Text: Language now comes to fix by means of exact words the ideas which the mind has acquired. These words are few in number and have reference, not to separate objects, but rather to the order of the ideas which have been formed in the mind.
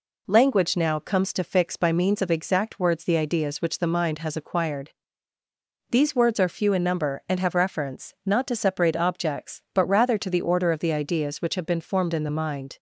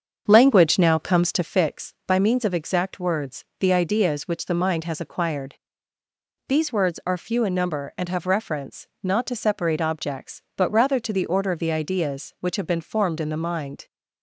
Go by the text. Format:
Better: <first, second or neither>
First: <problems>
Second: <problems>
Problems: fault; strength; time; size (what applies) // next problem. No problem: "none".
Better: first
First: none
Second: starts louder than the rest; until 1.8 s; 7 dB // pauses between "words" and "the"; slight; at 3.4 s; 0.16 s long